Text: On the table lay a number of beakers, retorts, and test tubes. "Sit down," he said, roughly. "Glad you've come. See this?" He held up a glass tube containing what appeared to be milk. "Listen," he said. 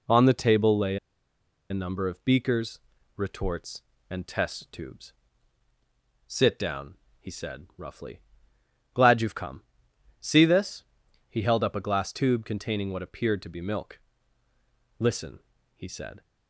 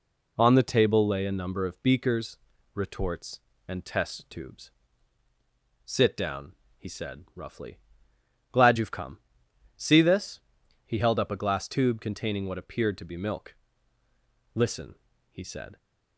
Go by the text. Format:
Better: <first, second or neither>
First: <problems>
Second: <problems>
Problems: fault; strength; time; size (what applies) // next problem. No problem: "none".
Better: second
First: pauses between "lay" and "a"; noticeable; at 0.9 s; 0.74 s long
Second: none